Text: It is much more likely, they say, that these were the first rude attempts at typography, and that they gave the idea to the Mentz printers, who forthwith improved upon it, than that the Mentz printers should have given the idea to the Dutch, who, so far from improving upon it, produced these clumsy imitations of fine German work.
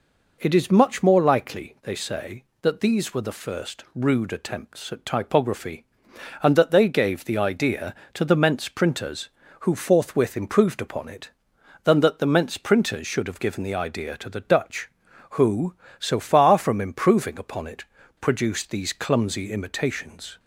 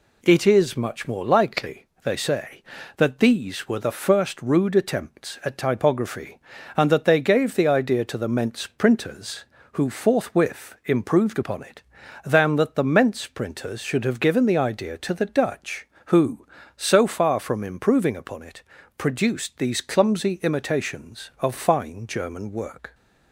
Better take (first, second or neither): second